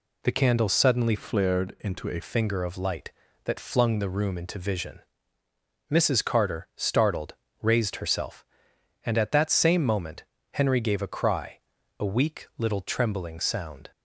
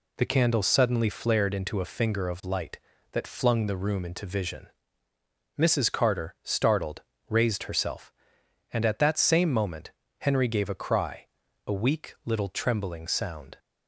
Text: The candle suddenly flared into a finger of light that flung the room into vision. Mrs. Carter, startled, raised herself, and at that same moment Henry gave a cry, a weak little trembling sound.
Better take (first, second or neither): second